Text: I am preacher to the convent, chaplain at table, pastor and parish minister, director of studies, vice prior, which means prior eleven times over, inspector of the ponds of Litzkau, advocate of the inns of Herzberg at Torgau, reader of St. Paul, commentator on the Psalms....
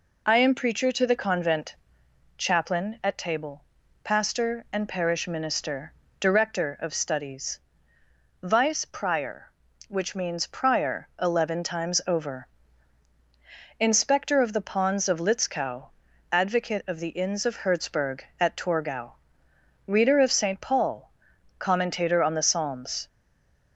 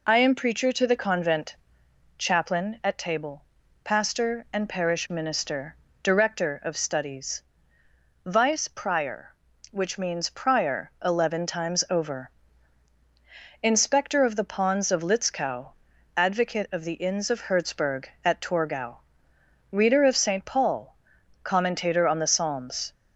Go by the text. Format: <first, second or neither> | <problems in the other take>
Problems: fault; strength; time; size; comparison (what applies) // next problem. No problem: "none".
second | stays silent after the last word; slight; from 23.0 s on; 0.7 s long